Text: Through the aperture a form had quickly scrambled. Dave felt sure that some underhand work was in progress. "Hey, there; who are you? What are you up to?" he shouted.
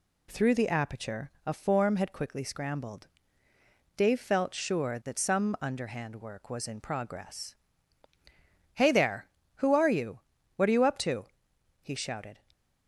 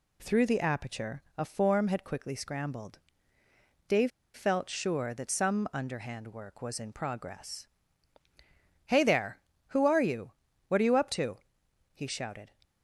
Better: first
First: none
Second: pauses between "Dave" and "felt"; slight; at 4.1 s; 0.23 s long

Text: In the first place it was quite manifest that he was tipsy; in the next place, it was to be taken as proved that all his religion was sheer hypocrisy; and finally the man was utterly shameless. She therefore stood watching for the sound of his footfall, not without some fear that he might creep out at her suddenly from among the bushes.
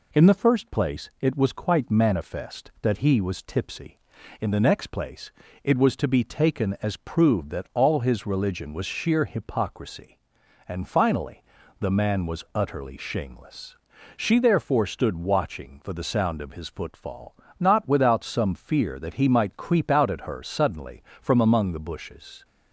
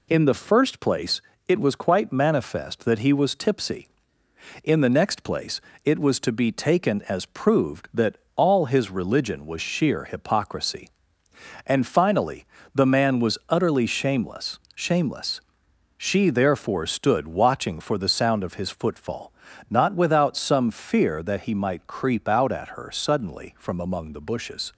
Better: first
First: pauses between "finally" and "the"; at 11.4 s; 0.38 s long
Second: pauses between "place" and "it"; slight; at 1.2 s; 0.26 s long // pauses between "that" and "all"; slight; at 8.1 s; 0.20 s long // pauses between "finally" and "the"; slight; at 12.4 s; 0.28 s long // says "shameless" twice; at 14.7 s

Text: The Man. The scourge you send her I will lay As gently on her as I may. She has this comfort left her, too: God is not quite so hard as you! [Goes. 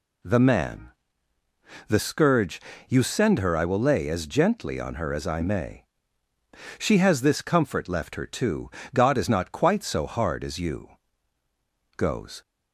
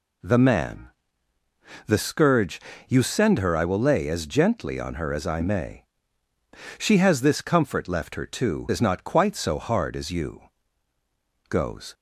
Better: first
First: pauses between "scourge" and "you"; slight; at 2.6 s; 0.28 s long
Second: pauses between "scourge" and "you"; slight; at 2.6 s; 0.28 s long // skips "God"; at 8.7 s

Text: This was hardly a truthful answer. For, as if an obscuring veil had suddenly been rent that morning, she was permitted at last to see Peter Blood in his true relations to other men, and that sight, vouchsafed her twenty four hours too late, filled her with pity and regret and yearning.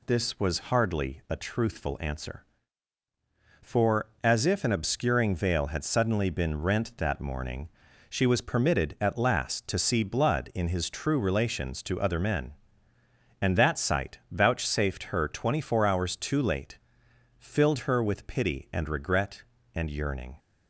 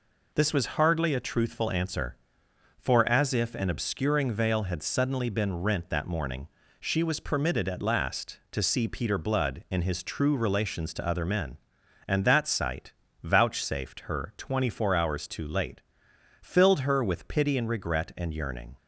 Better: second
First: skips "Peter"; at 10.0 s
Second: none

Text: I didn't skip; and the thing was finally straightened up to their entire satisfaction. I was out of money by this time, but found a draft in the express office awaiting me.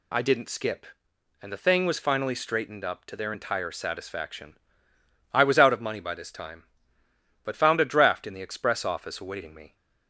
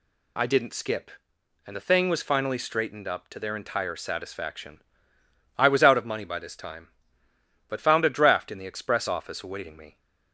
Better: neither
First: none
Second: none

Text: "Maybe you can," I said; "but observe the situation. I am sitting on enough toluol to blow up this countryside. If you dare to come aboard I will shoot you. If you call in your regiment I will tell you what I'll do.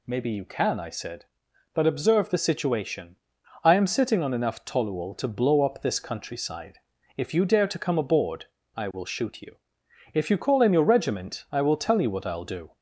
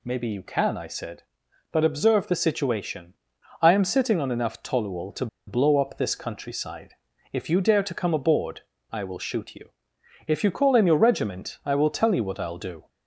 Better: first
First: pauses between "aboard" and "I"; slight; at 8.4 s; 0.28 s long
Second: pauses between "to" and "blow"; slight; at 5.2 s; 0.20 s long // pauses between "aboard" and "I"; slight; at 8.6 s; 0.28 s long

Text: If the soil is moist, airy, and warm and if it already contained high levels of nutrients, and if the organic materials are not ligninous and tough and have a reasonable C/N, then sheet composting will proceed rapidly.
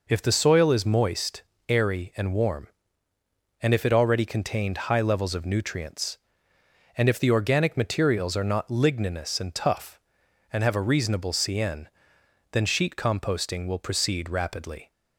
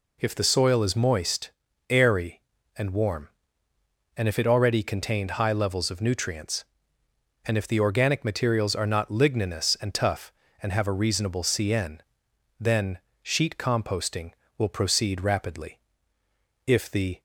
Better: first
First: none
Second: pauses between "then" and "sheet"; slight; at 12.9 s; 0.24 s long // goes on to say "If the"; from 16.6 s on; 0.54 s long

